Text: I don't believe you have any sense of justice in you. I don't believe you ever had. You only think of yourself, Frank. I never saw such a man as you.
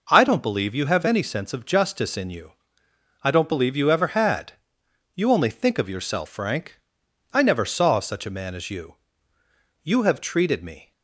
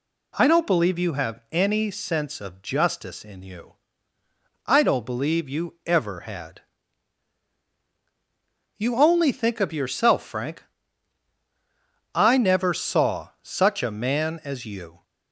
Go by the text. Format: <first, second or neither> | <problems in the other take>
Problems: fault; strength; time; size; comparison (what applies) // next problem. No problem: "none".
second | goes on to say "You have treated me"; noticeable; from 9.8 s on; 1.0 s long